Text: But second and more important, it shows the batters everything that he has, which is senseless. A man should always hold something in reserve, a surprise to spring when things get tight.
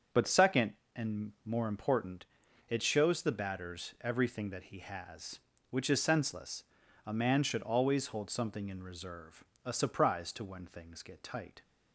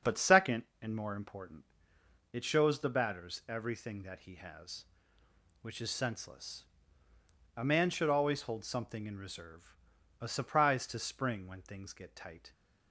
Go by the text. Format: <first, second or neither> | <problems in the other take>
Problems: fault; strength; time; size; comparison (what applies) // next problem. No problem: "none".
second | starts louder than the rest; until 1.5 s; 7 dB; also in the second // skips "spring"; at 10.4 s